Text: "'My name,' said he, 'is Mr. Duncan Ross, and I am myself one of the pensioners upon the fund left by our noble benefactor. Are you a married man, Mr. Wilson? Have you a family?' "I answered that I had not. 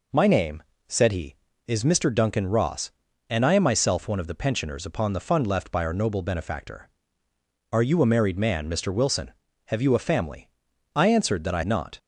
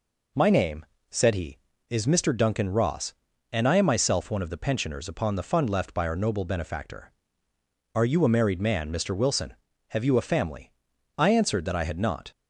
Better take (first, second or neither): second